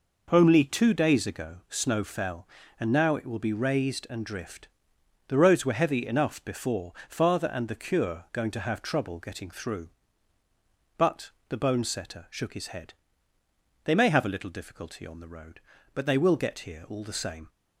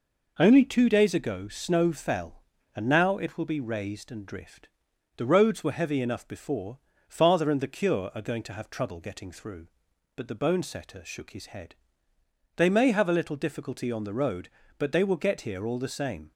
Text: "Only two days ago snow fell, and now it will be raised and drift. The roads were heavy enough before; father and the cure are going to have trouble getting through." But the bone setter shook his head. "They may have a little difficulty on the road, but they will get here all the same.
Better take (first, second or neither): second